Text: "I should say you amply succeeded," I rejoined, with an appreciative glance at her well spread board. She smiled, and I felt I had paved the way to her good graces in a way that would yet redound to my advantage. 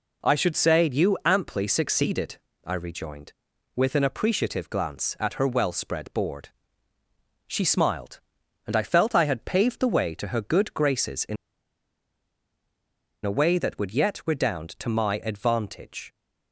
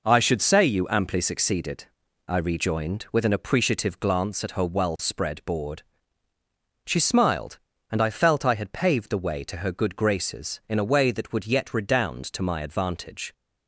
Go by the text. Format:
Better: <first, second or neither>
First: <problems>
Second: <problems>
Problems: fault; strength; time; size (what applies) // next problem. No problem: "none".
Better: second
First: pauses between "in" and "a"; strong; at 11.3 s; 1.9 s long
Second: none